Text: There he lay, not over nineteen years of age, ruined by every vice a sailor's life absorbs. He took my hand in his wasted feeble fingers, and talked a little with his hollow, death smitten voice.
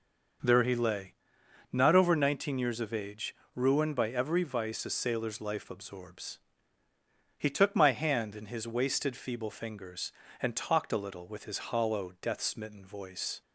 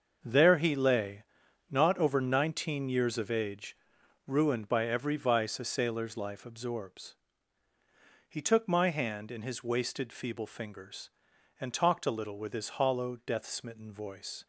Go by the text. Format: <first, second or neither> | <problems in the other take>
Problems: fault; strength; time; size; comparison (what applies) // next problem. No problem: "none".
first | gets quieter; strong; throughout; 10.5 dB // starts louder than the rest; until 1.2 s; 6.5 dB; noticeable in the first